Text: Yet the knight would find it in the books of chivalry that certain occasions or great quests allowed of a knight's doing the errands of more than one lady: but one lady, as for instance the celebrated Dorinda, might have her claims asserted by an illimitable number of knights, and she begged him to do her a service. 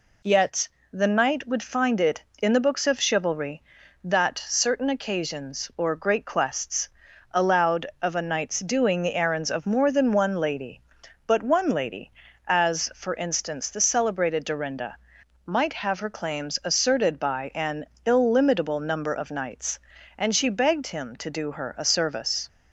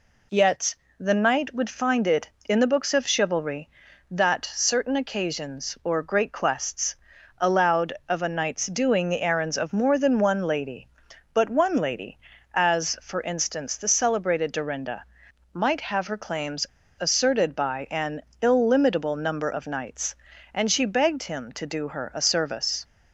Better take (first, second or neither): first